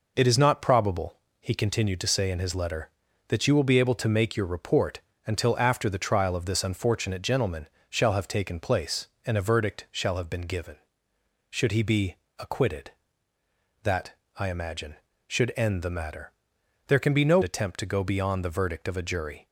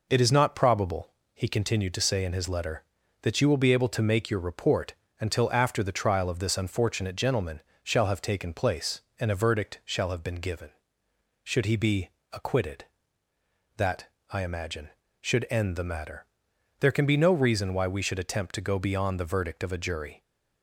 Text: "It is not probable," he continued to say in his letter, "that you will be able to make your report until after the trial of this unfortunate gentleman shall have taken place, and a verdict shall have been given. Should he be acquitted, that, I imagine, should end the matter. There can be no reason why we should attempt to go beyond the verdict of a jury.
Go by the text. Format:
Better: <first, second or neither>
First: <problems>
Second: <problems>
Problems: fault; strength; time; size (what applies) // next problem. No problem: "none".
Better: second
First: pauses between "report" and "until"; slight; at 5.0 s; 0.26 s long // pauses between "gentleman" and "shall"; slight; at 7.6 s; 0.22 s long // pauses between "be" and "acquitted"; slight; at 12.1 s; 0.22 s long // skips "reason why we should"; at 17.4 s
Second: pauses between "report" and "until"; slight; at 4.9 s; 0.26 s long // pauses between "gentleman" and "shall"; slight; at 7.6 s; 0.22 s long // pauses between "be" and "acquitted"; slight; at 12.0 s; 0.22 s long